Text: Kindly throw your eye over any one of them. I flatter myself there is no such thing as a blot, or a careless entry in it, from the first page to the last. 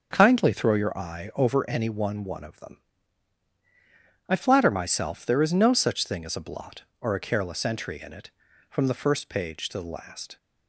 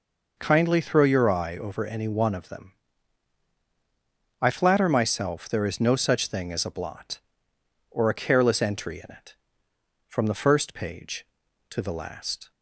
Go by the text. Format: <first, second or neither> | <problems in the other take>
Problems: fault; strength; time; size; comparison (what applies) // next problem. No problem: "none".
second | starts louder than the rest; until 1.1 s; 7 dB // says "one" twice; at 2.2 s